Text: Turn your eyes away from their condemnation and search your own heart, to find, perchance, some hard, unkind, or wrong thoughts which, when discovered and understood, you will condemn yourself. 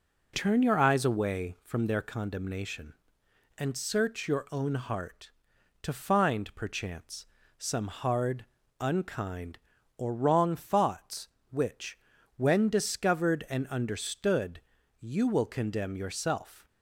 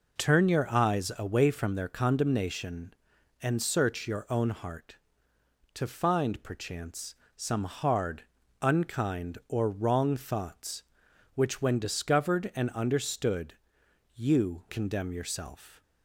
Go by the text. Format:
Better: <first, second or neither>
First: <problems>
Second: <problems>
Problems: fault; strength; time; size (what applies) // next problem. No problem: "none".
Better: first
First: none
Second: skips "will"; at 14.6 s